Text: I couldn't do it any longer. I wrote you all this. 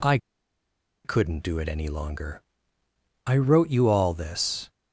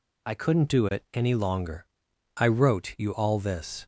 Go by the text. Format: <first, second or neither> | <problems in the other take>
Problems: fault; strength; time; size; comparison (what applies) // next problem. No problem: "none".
second | pauses between "I" and "couldn't"; noticeable; at 0.1 s; 0.87 s long